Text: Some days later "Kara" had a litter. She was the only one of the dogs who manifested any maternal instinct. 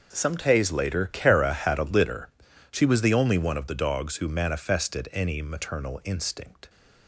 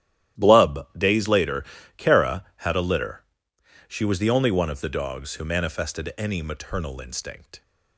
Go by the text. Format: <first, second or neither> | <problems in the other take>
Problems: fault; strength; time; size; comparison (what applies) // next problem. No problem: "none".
first | starts louder than the rest; strong; until 1.5 s; 12.5 dB // says "Blub" for "Some"; at 0.3 s // pauses between "later" and "Kara"; slight; at 1.6 s; 0.32 s long